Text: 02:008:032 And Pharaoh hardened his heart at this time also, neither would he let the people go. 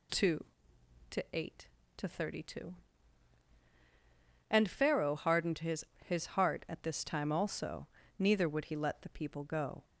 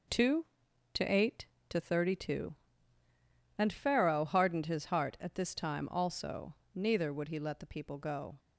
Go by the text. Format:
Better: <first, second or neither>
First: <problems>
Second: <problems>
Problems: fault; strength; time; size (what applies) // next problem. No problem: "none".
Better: second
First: says "his" twice; at 6.0 s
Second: none